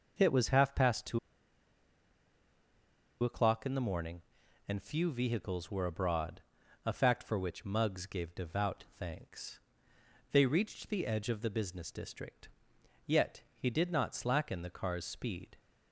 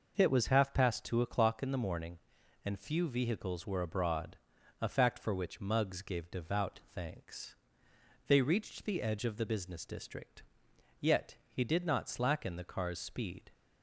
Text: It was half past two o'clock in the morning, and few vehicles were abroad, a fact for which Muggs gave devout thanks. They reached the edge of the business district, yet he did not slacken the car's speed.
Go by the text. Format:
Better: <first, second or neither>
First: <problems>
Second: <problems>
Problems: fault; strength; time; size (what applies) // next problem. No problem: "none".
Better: second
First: pauses between "two" and "o'clock"; strong; at 1.1 s; 2.0 s long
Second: none